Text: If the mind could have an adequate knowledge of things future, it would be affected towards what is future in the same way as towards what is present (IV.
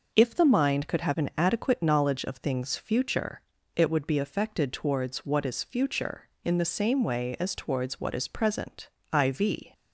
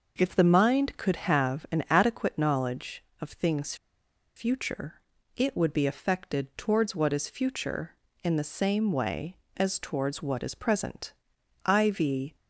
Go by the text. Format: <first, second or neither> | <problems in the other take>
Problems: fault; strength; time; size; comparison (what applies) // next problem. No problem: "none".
first | pauses between "things" and "future"; noticeable; at 3.7 s; 0.61 s long